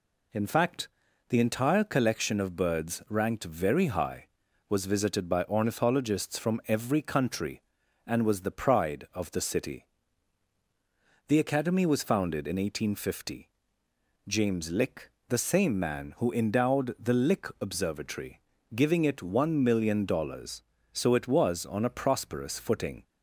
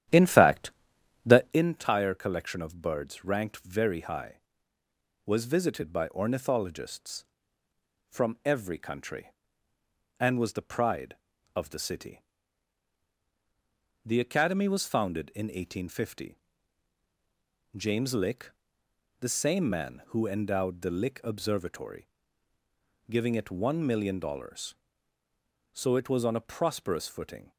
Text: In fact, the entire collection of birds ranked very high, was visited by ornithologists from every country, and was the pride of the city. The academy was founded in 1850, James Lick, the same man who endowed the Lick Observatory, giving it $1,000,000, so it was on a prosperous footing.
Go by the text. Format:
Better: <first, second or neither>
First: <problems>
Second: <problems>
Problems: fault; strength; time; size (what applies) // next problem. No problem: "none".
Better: first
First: none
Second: starts louder than the rest; strong; until 1.7 s; 11 dB